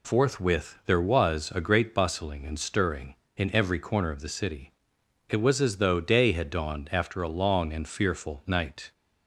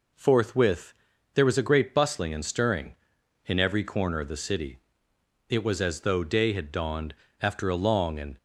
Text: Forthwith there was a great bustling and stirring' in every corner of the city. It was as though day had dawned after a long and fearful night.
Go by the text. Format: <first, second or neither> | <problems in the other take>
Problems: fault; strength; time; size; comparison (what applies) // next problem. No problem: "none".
first | pauses between "Forthwith" and "there"; at 0.9 s; 0.40 s long // pauses between "dawned" and "after"; slight; at 7.1 s; 0.24 s long // stops before "fearful night"; at 8.3 s